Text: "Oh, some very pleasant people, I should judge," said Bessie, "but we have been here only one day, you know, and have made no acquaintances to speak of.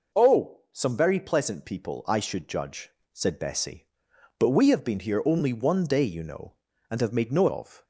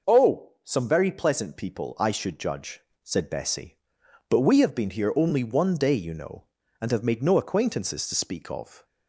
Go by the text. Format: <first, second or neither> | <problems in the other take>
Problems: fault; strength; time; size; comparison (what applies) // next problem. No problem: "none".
second | skips "acquaintances to speak"; at 7.4 s